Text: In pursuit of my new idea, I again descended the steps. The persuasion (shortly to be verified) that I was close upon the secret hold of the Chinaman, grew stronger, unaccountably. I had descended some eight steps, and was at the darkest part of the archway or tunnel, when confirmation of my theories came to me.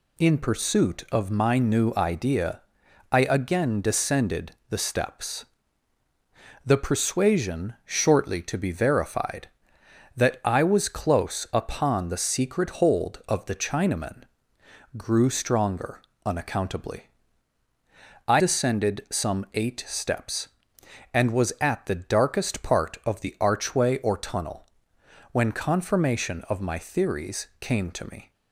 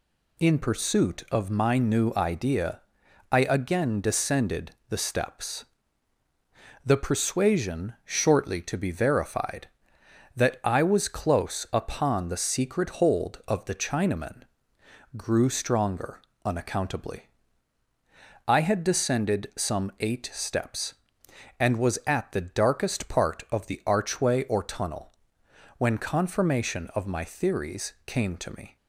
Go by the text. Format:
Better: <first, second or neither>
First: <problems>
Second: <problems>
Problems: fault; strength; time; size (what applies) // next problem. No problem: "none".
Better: second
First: pauses between "descended" and "the"; slight; at 4.5 s; 0.18 s long // skips "had"; at 18.4 s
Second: pauses between "descended" and "the"; slight; at 4.7 s; 0.18 s long